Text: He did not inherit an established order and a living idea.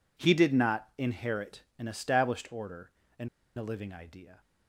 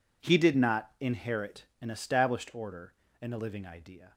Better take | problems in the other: second | pauses between "inherit" and "an"; slight; at 1.6 s; 0.16 s long; slight in the second // pauses between "and" and "a"; slight; at 3.2 s; 0.29 s long

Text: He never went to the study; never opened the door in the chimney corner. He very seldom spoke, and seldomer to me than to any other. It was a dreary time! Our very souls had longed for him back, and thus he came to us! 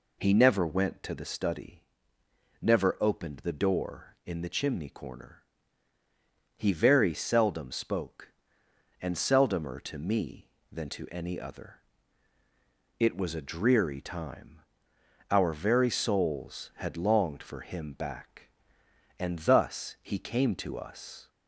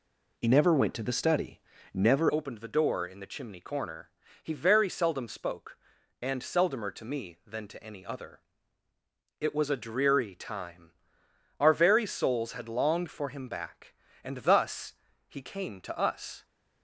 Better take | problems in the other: first | changes voice at "opened"; from 2.3 s on; 14.1 s long // pauses between "thus" and "he"; slight; at 14.9 s; 0.32 s long

